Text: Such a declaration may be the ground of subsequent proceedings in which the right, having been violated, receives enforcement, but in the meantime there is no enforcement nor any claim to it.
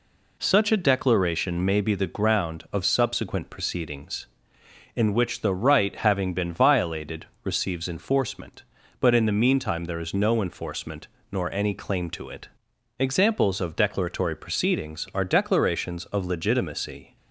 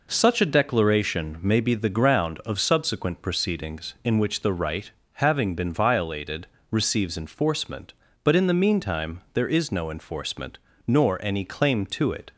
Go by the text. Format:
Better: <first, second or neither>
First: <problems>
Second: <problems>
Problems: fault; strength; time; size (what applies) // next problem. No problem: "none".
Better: second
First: pauses between "enforcement" and "nor"; slight; at 11.0 s; 0.24 s long // goes on to say "Examples of declaratory proceedings are declarations of legitimacy"; strong; from 12.9 s on; 4.1 s long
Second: pauses between "enforcement" and "nor"; slight; at 10.5 s; 0.30 s long